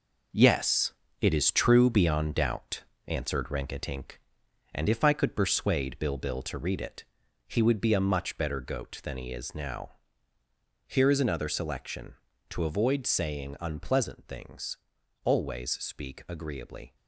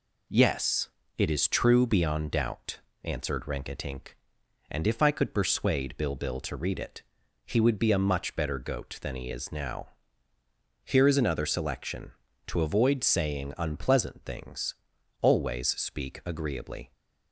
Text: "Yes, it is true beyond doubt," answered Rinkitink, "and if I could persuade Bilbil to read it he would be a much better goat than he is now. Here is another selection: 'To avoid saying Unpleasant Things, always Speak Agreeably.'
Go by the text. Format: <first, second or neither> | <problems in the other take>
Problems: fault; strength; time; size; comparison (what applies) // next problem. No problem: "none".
second | gets quieter; strong; throughout; 8 dB // pauses between "it" and "he"; at 7.0 s; 0.42 s long; also in the second